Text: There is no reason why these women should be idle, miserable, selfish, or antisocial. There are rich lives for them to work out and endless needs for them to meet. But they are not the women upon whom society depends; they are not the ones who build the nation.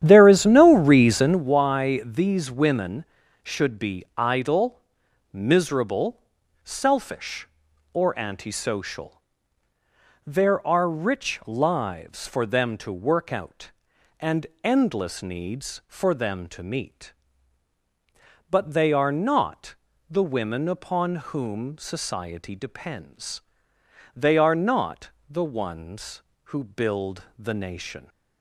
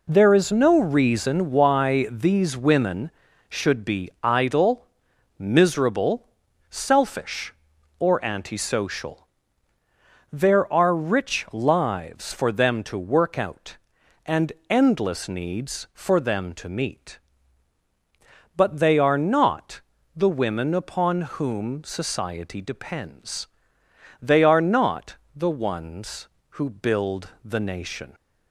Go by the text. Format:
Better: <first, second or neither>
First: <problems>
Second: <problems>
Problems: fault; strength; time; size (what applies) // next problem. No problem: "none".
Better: second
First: starts louder than the rest; strong; until 1.5 s; 10.5 dB // pauses between "and" and "endless"; slight; at 14.4 s; 0.20 s long // pauses between "not" and "the"; slight; at 19.7 s; 0.36 s long // pauses between "upon" and "whom"; slight; at 21.1 s; 0.16 s long // pauses between "not" and "the"; slight; at 25.1 s; 0.20 s long // pauses between "build" and "the"; slight; at 27.2 s; 0.16 s long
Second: pauses between "and" and "endless"; slight; at 14.5 s; 0.20 s long // pauses between "not" and "the"; slight; at 19.8 s; 0.36 s long // pauses between "upon" and "whom"; slight; at 21.2 s; 0.16 s long // pauses between "not" and "the"; slight; at 25.1 s; 0.20 s long // pauses between "build" and "the"; slight; at 27.2 s; 0.16 s long